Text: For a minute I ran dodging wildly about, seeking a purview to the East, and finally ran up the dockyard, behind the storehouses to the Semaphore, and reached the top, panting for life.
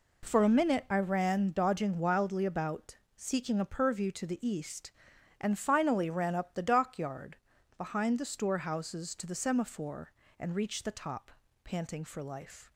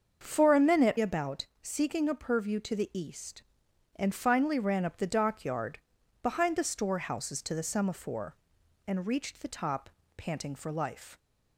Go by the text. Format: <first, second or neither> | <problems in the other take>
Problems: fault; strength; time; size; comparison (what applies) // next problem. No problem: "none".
first | starts louder than the rest; until 1.2 s; 6.5 dB // skips "I ran dodging wildly"; at 0.9 s